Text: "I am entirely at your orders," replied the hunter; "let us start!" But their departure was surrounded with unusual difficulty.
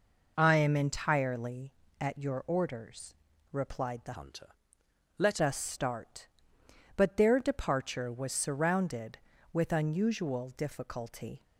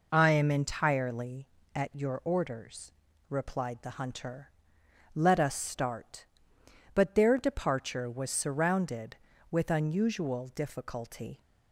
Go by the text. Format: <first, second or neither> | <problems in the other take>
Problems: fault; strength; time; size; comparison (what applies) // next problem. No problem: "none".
second | changes voice from "hunter" to "let"; from 4.1 to 5.3 s; 1.2 s long